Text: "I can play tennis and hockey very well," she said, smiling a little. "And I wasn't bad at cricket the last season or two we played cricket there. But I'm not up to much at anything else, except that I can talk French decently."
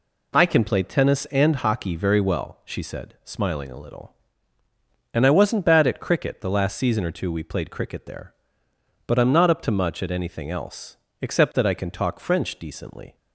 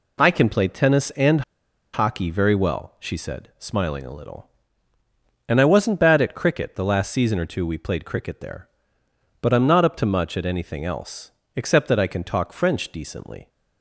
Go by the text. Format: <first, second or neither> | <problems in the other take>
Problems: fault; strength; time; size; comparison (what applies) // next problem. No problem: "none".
first | pauses between "and" and "hockey"; noticeable; at 1.4 s; 0.52 s long